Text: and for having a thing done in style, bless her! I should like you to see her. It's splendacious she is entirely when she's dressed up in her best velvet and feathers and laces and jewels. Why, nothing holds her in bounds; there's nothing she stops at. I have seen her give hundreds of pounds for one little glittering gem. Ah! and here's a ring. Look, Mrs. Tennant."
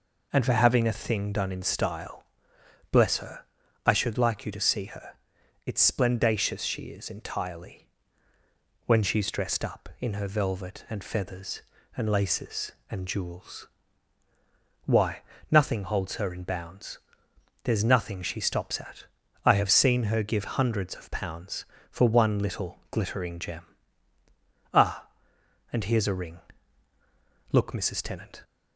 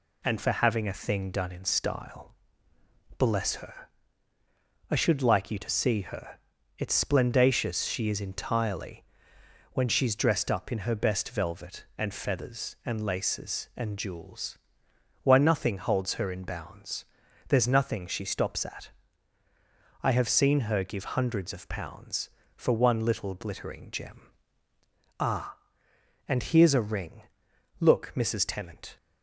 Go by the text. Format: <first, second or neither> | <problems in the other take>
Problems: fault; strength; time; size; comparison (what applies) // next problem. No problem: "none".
second | pauses between "entirely" and "when"; at 7.8 s; 1.0 s long; noticeable in the second // skips "best"; at 10.2 s